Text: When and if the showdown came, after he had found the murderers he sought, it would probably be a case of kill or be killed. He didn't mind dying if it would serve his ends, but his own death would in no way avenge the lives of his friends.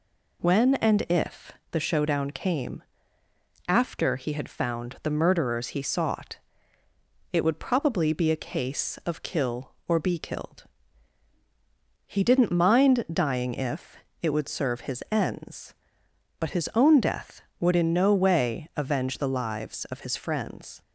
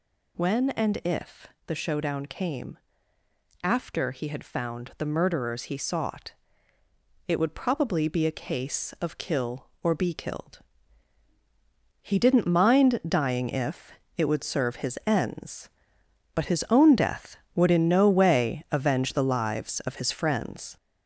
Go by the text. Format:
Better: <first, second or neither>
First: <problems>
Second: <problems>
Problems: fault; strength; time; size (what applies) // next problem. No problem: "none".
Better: first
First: pauses between "if" and "the"; slight; at 1.5 s; 0.18 s long // pauses between "if" and "it"; slight; at 13.9 s; 0.26 s long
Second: gets louder; noticeable; throughout; 4.5 dB // pauses between "if" and "the"; slight; at 1.4 s; 0.18 s long // pauses between "if" and "it"; slight; at 13.9 s; 0.26 s long